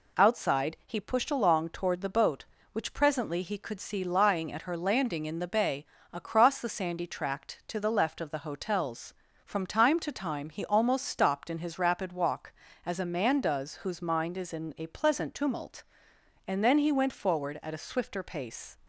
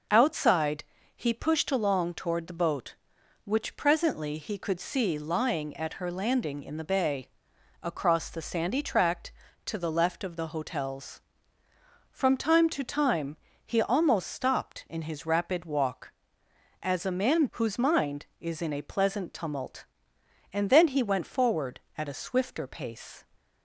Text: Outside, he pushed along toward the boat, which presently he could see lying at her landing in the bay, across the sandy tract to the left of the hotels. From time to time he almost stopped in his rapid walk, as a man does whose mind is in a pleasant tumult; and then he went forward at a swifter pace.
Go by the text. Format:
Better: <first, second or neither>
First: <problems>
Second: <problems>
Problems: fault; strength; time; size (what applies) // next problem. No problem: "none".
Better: first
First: none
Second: pauses between "time" and "he"; slight; at 13.3 s; 0.30 s long // skips "does"; at 17.4 s